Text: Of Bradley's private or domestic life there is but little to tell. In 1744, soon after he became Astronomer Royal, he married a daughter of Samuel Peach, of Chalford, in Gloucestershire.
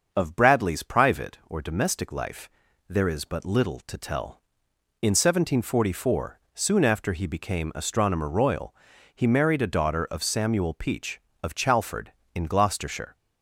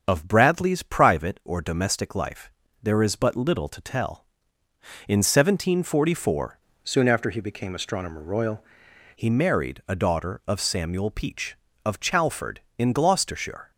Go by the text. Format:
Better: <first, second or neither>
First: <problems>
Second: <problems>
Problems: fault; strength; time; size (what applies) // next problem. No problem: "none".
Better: first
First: starts louder than the rest; until 1.1 s; 6.5 dB // pauses between "life" and "there"; at 2.4 s; 0.40 s long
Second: starts louder than the rest; until 1.0 s; 7 dB // pauses between "life" and "there"; slight; at 2.5 s; 0.32 s long // changes voice from "soon" to "Royal"; from 6.8 to 8.6 s; 1.8 s long